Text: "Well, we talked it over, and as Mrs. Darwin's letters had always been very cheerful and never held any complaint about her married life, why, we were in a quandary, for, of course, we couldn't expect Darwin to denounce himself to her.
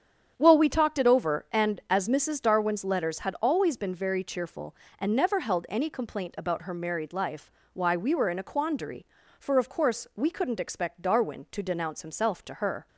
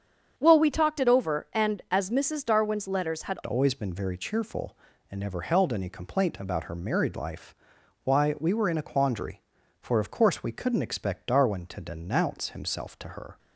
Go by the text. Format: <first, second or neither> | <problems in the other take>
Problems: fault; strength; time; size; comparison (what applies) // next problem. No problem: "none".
first | starts louder than the rest; strong; until 1.3 s; 7.5 dB; strong in the first // changes voice at "always"; from 3.4 s on; 9.9 s long